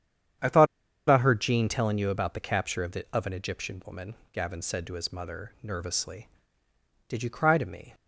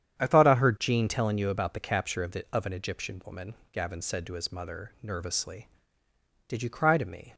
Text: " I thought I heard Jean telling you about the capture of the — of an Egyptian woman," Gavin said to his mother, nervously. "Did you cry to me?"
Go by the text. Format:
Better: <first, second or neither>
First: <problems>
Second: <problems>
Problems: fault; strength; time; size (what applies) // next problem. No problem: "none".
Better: second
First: starts louder than the rest; strong; until 1.8 s; 8.5 dB // pauses between "thought" and "I"; at 0.6 s; 0.43 s long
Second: starts louder than the rest; strong; until 1.2 s; 9 dB